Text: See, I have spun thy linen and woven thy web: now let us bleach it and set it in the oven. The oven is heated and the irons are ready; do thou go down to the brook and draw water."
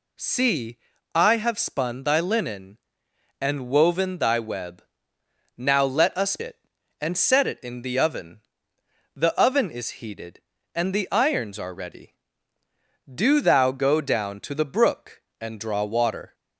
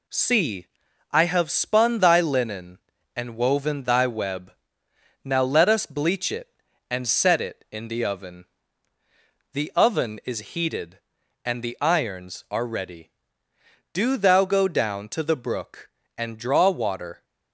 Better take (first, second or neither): second